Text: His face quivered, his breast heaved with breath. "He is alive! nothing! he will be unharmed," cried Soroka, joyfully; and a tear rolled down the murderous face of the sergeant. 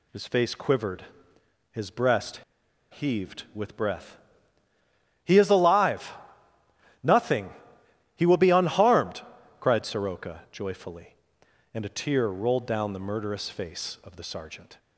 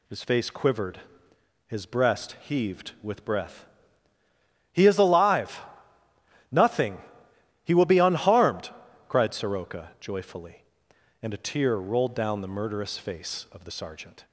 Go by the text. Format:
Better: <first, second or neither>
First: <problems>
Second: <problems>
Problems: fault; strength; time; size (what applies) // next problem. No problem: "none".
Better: second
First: pauses between "breast" and "heaved"; noticeable; at 2.4 s; 0.53 s long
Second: none